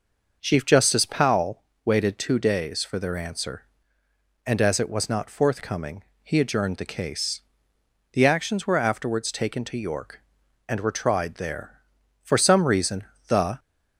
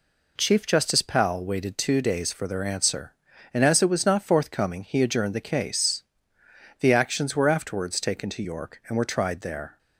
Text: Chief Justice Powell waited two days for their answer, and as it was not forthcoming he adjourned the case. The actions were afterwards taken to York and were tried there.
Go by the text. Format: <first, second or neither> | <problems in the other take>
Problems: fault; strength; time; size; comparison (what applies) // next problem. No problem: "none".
second | pauses between "Powell" and "waited"; slight; at 1.6 s; 0.22 s long // pauses between "forthcoming" and "he"; slight; at 6.0 s; 0.20 s long // goes on to say "For some reason the"; from 12.2 s on; 1.3 s long